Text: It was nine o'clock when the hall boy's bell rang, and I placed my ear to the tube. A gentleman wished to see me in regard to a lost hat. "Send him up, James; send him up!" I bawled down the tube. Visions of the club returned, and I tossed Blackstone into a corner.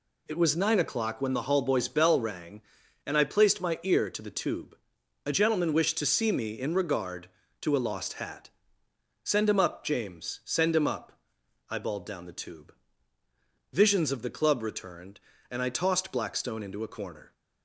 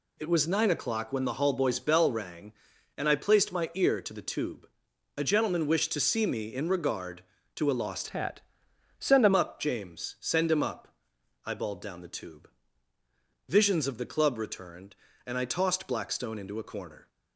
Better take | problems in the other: first | changes voice from "hat" to "him"; from 8.0 to 9.3 s; 1.3 s long

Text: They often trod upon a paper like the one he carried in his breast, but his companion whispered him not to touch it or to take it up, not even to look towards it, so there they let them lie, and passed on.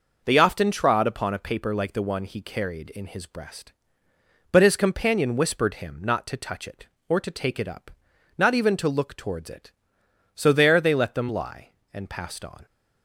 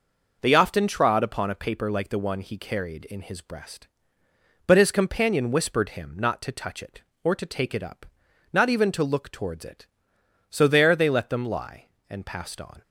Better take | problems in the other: neither | none

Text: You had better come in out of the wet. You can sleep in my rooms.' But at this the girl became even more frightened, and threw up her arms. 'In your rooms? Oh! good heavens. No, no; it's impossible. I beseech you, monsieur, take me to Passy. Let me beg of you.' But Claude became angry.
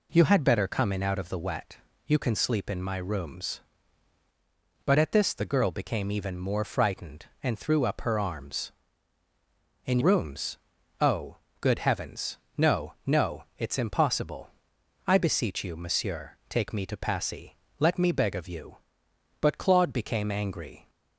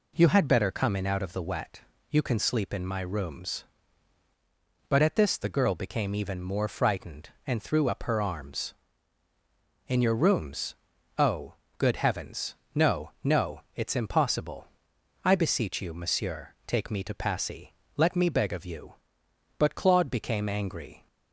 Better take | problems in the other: second | skips "your"; at 10.0 s

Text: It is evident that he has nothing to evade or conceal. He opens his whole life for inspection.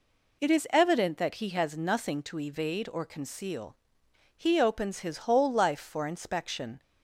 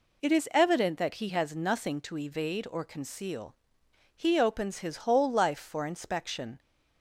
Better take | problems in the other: neither | none

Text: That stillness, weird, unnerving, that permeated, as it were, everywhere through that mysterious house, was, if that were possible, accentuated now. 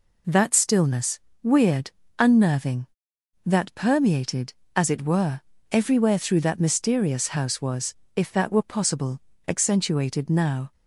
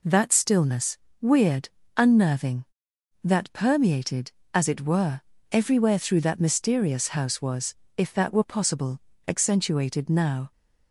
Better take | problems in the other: neither | none

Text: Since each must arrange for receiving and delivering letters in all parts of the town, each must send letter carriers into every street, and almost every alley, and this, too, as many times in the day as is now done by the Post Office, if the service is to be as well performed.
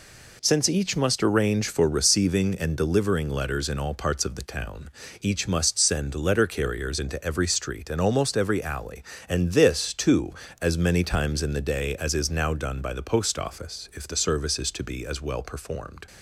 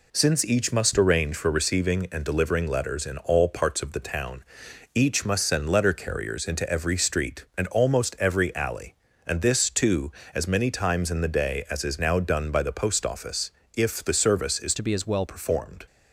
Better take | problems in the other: first | changes voice from "to" to "well"; from 14.7 to 15.2 s; 0.5 s long

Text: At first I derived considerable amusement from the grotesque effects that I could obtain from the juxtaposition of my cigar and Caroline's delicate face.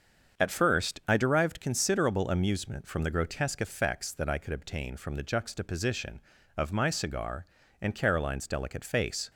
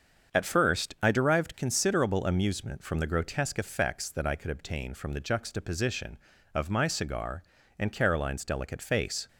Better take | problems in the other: neither | starts louder than the rest; the same in both

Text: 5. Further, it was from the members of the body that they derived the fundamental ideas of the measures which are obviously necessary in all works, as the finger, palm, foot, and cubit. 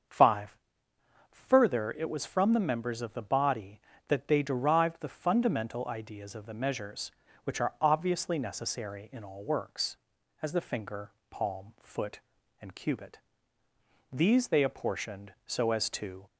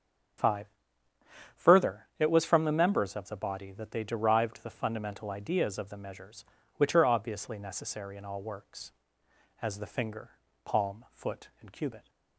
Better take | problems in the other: second | starts louder than the rest; until 1.8 s; 7 dB; strong in the second // goes on to say "These they apportioned so as to"; strong; from 14.1 s on; 2.1 s long

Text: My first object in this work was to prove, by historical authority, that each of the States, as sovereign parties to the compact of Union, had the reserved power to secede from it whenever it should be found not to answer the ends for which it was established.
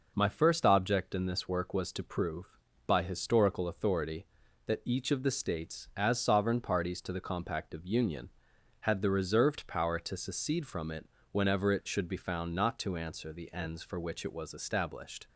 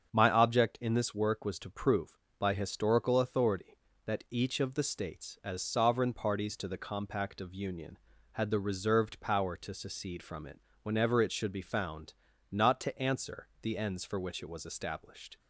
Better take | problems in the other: first | starts louder than the rest; strong; until 1.1 s; 7.5 dB // skips "first"; at 0.3 s // pauses between "it" and "whenever"; slight; at 10.6 s; 0.22 s long; slight in the first // pauses between "found" and "not"; slight; at 12.1 s; 0.36 s long

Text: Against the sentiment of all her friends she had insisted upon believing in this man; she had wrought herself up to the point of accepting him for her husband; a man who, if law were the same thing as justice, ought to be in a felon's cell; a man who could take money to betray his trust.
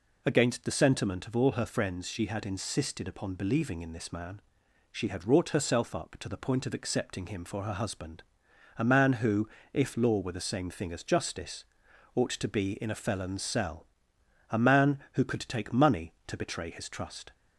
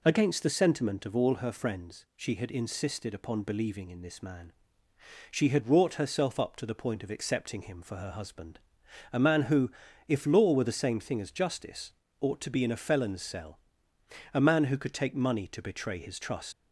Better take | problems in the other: first | leaves "trust" unfinished; at 16.5 s; 115 ms

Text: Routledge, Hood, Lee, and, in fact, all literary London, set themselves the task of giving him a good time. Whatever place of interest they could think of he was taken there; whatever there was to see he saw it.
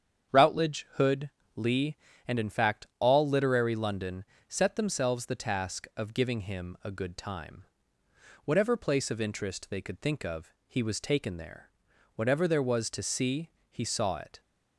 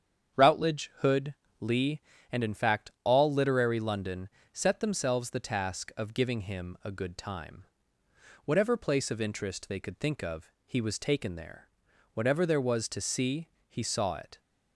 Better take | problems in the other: neither | starts louder than the rest; strong; the same in both // pauses between "of" and "he"; slight; the same in both // pauses between "see" and "he"; slight; the same in both

